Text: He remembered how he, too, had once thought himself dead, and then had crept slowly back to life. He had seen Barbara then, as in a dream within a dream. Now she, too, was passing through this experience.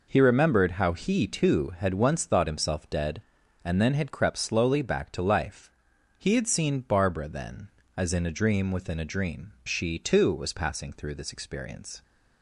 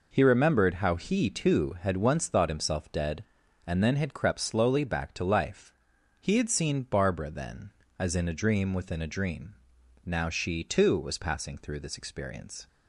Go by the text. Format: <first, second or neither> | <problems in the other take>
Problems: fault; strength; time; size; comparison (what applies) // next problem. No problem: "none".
second | skips "Now"; at 9.5 s